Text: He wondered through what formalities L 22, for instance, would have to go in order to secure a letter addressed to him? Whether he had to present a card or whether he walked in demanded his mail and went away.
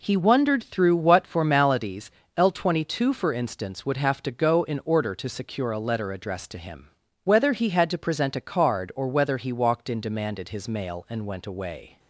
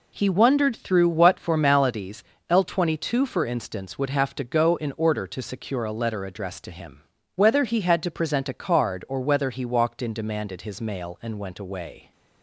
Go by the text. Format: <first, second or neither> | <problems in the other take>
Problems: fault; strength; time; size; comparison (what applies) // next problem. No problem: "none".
neither | pauses between "formalities" and "L"; slight; the same in both